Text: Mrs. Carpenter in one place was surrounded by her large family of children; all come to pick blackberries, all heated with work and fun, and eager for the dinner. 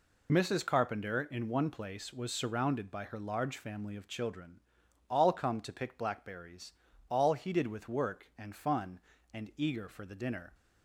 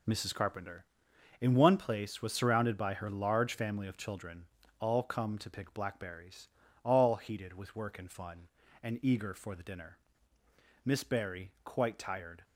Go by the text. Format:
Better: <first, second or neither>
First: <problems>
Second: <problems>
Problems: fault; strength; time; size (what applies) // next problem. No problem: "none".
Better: first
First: none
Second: goes on to say "Miss Barry quite tired"; from 10.8 s on; 1.5 s long